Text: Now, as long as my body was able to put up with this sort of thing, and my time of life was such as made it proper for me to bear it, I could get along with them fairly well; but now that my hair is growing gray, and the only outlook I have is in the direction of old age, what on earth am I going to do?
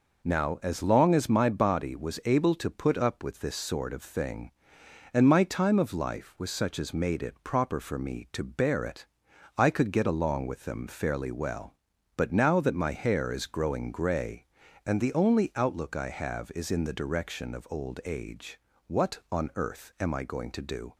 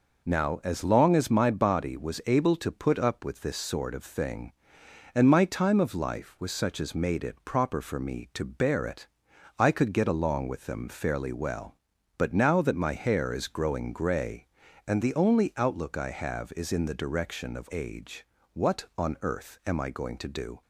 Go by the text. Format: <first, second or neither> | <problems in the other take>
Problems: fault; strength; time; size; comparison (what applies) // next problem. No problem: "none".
first | skips "old"; at 17.6 s